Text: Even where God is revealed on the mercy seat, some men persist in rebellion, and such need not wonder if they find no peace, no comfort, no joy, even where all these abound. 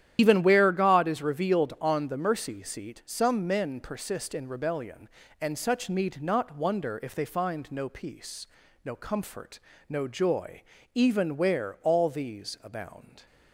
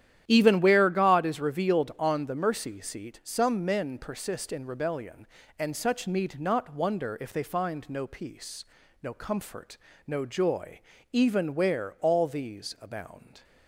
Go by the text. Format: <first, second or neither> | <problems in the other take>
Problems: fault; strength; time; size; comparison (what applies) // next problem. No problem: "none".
second | loses the start of "Even"; at 0.1 s; 95 ms // starts louder than the rest; strong; until 1.1 s; 11 dB; strong in the second